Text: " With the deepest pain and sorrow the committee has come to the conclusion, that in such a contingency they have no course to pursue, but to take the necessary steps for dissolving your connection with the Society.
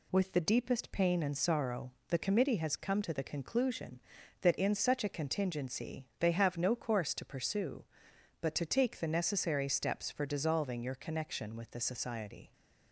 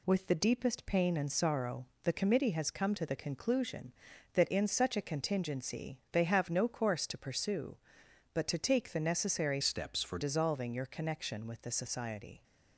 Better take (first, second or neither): first